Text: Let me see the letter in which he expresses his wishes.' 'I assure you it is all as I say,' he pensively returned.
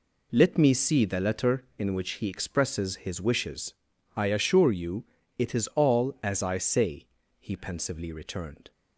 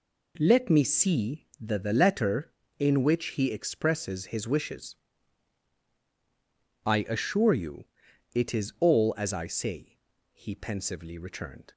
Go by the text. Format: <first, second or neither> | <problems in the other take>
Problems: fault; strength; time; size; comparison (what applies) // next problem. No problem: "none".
first | says "the" twice; at 1.7 s // pauses between "you" and "it"; noticeable; at 7.8 s; 0.48 s long; slight in the first